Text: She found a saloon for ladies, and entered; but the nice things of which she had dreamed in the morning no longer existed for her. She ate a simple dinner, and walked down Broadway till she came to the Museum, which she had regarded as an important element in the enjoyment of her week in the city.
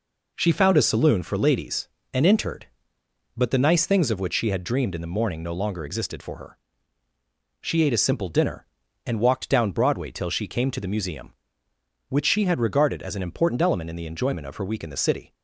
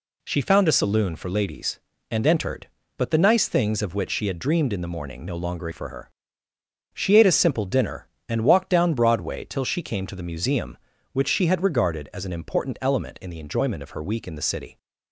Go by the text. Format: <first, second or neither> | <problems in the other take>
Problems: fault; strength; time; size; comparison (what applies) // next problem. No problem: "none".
first | skips "existed"; at 5.7 s